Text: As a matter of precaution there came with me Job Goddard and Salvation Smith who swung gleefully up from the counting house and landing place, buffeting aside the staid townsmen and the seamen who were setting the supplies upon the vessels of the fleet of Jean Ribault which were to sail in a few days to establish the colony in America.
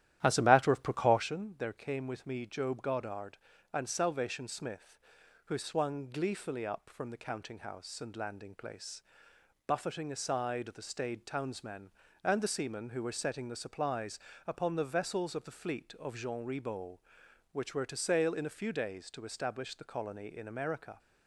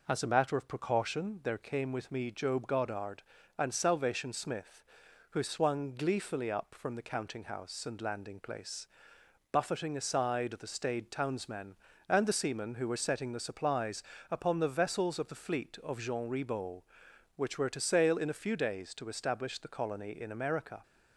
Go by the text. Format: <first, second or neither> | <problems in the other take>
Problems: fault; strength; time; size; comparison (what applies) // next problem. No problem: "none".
second | starts louder than the rest; strong; until 1.3 s; 12 dB // pauses between "supplies" and "upon"; slight; at 14.1 s; 0.30 s long; slight in the second